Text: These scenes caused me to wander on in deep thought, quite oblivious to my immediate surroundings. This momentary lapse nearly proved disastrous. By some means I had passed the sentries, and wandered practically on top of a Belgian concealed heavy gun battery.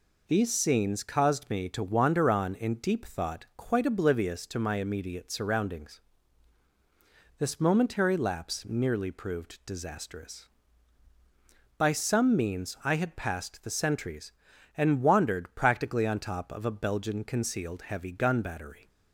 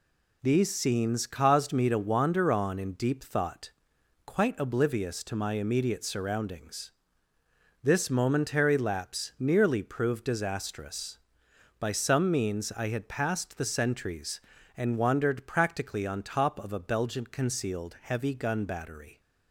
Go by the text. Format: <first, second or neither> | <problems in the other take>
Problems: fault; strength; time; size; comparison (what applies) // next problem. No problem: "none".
neither | none